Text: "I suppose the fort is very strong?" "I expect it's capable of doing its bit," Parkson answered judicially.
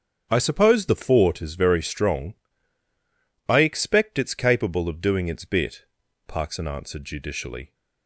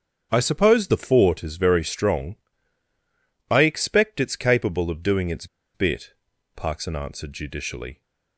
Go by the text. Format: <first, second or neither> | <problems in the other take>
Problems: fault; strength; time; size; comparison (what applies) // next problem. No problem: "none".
first | starts louder than the rest; strong; until 1.3 s; 7 dB; strong in the first // pauses between "its" and "bit"; slight; at 5.4 s; 0.29 s long